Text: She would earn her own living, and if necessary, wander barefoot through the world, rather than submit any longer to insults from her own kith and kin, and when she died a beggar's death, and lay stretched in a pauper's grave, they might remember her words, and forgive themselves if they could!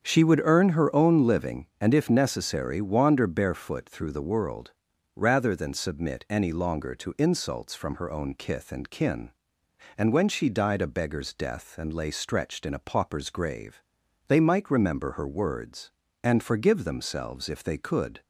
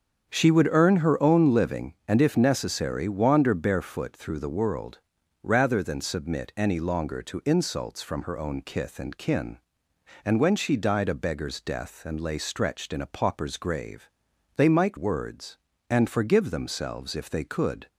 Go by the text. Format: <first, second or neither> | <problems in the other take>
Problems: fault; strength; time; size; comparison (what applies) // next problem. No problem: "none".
first | starts louder than the rest; strong; until 1.3 s; 7.5 dB; strong in the first // skips "remember her"; at 14.9 s